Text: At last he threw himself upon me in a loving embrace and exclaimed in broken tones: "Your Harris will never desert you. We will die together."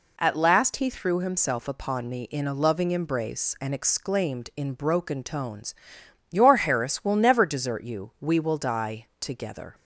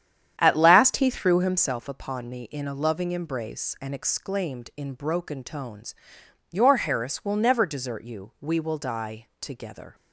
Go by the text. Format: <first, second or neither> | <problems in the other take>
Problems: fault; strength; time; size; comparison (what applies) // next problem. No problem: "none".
first | starts louder than the rest; strong; until 1.8 s; 9.5 dB